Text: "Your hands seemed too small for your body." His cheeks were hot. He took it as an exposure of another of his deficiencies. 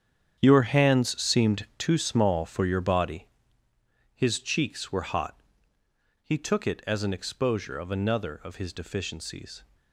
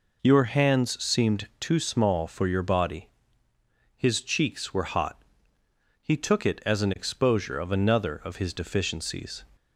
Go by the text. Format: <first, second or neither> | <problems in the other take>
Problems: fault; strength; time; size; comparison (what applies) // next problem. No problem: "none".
second | gets quieter; strong; throughout; 13 dB